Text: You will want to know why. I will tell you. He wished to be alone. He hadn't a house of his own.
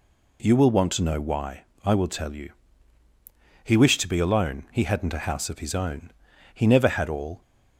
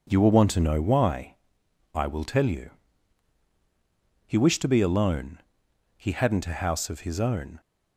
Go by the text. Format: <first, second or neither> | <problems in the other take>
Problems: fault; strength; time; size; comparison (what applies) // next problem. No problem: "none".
second | goes on to say "He never had all"; noticeable; from 6.5 s on; 0.86 s long